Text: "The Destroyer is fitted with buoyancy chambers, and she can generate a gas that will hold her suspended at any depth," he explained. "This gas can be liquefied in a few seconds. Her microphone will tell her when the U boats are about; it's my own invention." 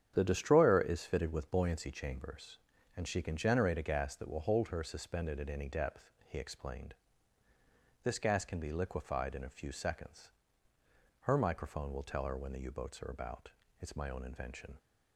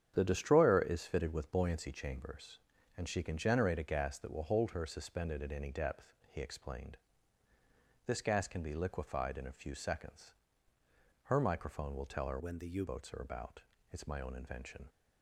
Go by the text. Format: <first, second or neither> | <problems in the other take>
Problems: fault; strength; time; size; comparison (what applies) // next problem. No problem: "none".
first | starts louder than the rest; strong; until 1.1 s; 9 dB; strong in the first // changes voice from "when" to "U"; from 12.3 to 12.8 s; 0.5 s long